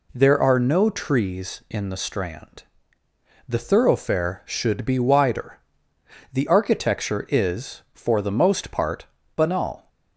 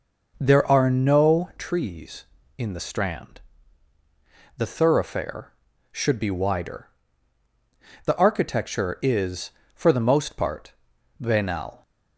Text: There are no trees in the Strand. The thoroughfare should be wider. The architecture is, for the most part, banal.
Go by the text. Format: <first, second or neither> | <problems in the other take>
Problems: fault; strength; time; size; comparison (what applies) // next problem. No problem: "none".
first | starts louder than the rest; noticeable; until 1.7 s; 5.5 dB